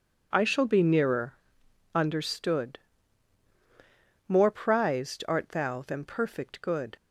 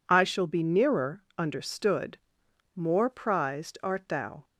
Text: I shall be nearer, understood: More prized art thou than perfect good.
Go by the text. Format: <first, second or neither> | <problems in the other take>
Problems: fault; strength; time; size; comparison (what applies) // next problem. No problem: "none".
first | stops before "than perfect good"; at 4.4 s